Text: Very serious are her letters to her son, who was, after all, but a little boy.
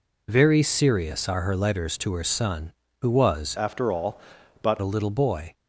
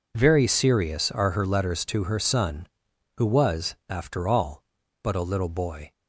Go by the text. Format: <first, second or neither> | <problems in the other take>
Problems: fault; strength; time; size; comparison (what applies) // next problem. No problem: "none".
second | changes voice from "after" to "but"; from 3.5 to 4.7 s; 1.2 s long